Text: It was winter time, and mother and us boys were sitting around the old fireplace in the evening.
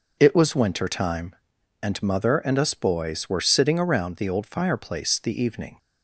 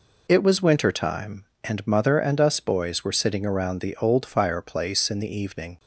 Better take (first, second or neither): second